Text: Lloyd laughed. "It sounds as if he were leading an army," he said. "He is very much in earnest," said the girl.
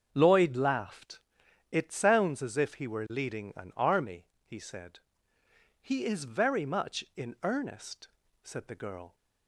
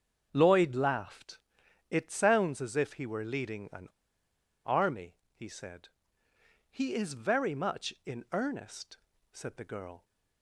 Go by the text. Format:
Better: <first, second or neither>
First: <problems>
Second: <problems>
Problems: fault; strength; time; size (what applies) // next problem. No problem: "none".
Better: first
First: starts louder than the rest; until 1.1 s; 7 dB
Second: starts louder than the rest; until 1.3 s; 7 dB // pauses between "an" and "army"; noticeable; at 3.8 s; 0.77 s long